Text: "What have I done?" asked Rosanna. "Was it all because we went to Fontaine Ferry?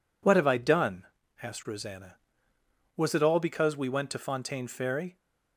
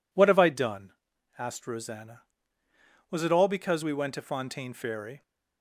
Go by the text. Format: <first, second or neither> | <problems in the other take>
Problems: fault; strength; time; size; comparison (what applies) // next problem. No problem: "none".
neither | none